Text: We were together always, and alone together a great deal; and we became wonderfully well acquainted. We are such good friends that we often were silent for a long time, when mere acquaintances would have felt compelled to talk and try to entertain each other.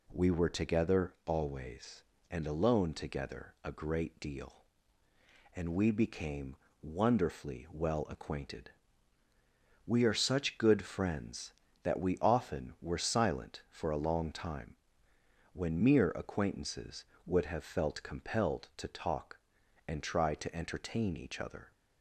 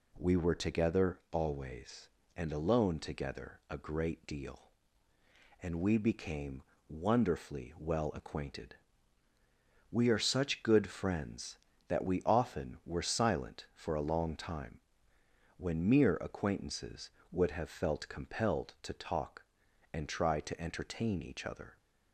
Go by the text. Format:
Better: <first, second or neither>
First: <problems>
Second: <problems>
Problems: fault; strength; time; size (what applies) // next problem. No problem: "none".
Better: neither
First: pauses between "became" and "wonderfully"; slight; at 6.5 s; 0.26 s long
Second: pauses between "became" and "wonderfully"; slight; at 6.6 s; 0.26 s long